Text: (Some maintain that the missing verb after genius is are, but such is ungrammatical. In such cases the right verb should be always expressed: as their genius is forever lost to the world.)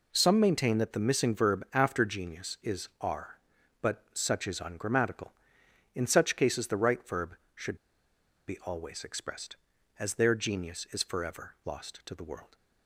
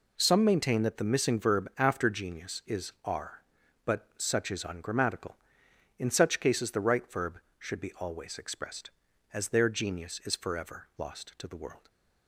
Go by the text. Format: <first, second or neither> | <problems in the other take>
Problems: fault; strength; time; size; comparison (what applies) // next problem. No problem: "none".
second | pauses between "should" and "be"; noticeable; at 7.7 s; 0.70 s long